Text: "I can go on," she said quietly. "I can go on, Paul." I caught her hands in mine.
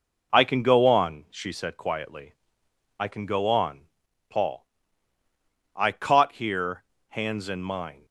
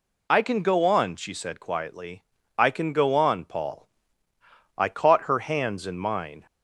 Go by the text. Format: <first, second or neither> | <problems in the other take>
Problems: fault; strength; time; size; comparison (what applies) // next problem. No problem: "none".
second | says "here" for "her"; at 6.3 s